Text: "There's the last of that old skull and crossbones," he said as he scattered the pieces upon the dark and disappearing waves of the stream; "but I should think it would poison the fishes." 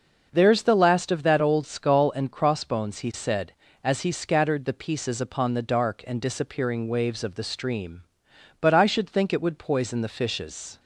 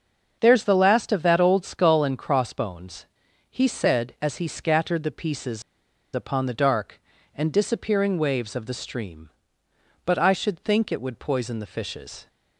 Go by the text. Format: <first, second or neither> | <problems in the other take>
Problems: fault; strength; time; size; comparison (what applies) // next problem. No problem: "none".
first | starts louder than the rest; until 1.4 s; 6.5 dB // pauses between "pieces" and "upon"; noticeable; at 5.6 s; 0.53 s long